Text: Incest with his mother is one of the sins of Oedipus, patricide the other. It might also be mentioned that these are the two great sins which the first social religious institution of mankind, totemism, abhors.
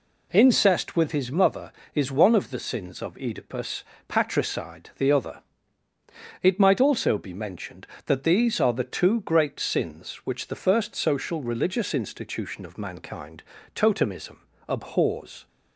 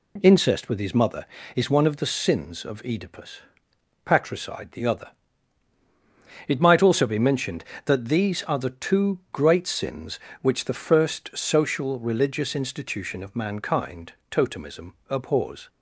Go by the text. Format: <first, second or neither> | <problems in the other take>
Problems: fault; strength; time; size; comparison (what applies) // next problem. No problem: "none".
neither | none